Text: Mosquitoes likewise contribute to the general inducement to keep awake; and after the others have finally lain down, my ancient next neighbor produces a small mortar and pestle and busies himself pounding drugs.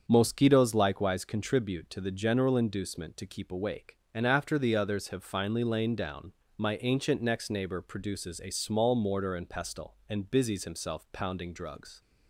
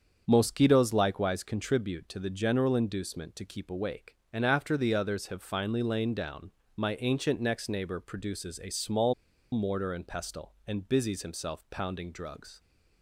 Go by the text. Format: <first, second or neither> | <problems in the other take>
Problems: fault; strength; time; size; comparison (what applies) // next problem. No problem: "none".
first | starts louder than the rest; strong; until 1.2 s; 7 dB; strong in the first // pauses between "small" and "mortar"; at 9.1 s; 0.40 s long